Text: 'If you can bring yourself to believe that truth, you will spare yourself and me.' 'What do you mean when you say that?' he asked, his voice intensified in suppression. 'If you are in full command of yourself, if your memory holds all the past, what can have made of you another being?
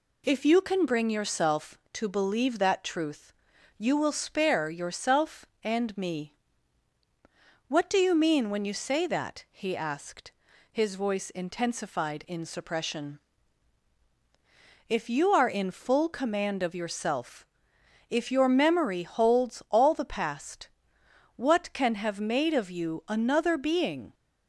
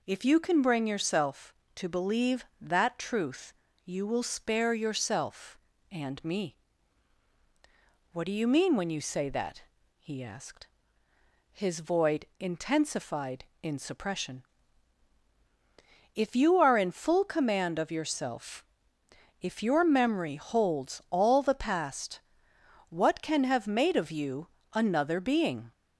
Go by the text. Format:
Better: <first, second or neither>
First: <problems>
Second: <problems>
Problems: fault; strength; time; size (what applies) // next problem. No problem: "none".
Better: first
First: none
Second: says "void" for "voice"; at 11.8 s // pauses between "you" and "another"; slight; at 24.4 s; 0.24 s long